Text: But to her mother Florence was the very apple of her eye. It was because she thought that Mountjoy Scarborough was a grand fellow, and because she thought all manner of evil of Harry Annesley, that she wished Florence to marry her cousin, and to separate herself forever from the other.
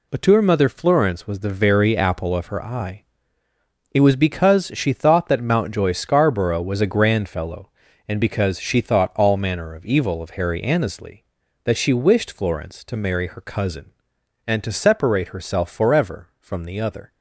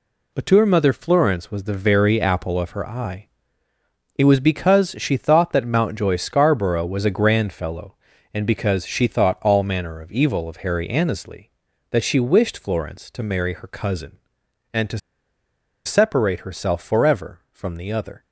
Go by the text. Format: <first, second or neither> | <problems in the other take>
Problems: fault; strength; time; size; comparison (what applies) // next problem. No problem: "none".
first | pauses between "to" and "separate"; noticeable; at 14.9 s; 0.87 s long